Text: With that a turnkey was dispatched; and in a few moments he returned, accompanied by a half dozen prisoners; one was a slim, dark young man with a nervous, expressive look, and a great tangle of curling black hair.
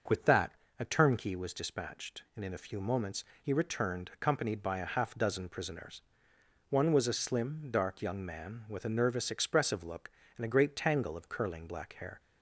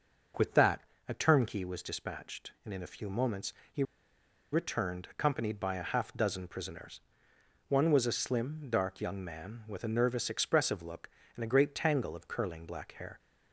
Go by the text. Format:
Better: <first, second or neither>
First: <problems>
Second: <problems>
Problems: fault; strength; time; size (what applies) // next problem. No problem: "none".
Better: first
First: starts louder than the rest; until 1.3 s; 6.5 dB // pauses between "that" and "a"; slight; at 0.5 s; 0.26 s long // pauses between "moments" and "he"; slight; at 3.2 s; 0.18 s long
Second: starts louder than the rest; until 1.6 s; 6.5 dB // pauses between "that" and "a"; slight; at 0.8 s; 0.26 s long // pauses between "moments" and "he"; slight; at 3.5 s; 0.18 s long // pauses between "he" and "returned"; noticeable; at 3.8 s; 0.68 s long